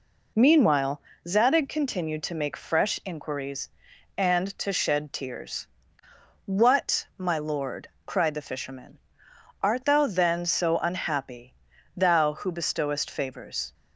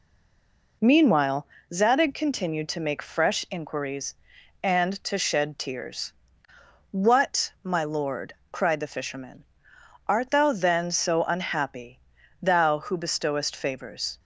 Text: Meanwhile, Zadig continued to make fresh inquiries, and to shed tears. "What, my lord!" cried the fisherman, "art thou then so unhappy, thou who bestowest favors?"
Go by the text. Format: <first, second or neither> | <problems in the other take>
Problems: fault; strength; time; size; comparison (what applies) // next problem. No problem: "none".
first | stays silent before the first word; slight; until 0.8 s; 0.8 s long